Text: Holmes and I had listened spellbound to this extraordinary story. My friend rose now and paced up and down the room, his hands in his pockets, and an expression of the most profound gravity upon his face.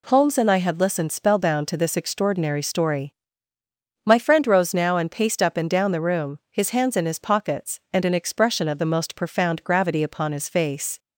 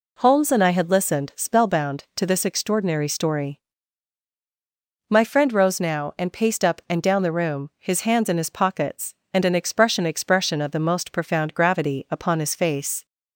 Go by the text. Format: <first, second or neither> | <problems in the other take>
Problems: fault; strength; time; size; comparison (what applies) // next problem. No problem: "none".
first | says "expression" twice; at 10.0 s